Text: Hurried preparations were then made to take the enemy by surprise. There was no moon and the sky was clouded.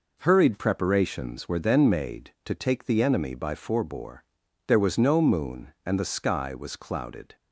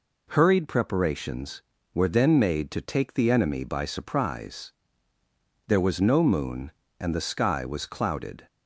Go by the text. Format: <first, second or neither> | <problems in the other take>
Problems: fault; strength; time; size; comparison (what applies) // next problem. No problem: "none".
second | says "forebore" for "surprise"; at 3.5 s